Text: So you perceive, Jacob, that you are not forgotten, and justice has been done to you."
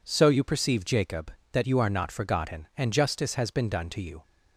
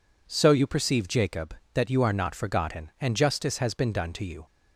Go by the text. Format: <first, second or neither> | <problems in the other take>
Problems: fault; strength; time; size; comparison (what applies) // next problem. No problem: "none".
neither | none